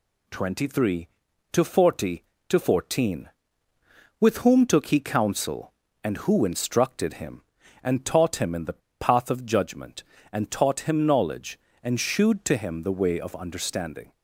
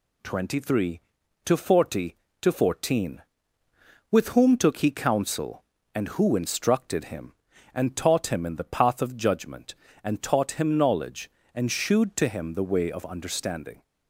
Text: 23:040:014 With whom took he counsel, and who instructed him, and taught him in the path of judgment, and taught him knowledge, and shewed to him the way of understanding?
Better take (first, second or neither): second